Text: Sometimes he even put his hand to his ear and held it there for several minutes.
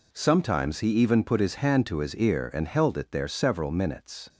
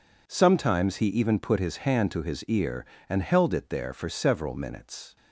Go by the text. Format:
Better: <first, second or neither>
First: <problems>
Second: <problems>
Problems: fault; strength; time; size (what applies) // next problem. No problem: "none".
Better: second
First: skips "for"; at 3.2 s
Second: none